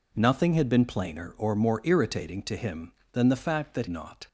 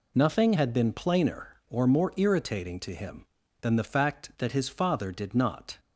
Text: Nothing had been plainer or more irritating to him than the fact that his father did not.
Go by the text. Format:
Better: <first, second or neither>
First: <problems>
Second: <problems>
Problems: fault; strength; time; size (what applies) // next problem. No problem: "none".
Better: second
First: skips "his father did"; at 3.8 s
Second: none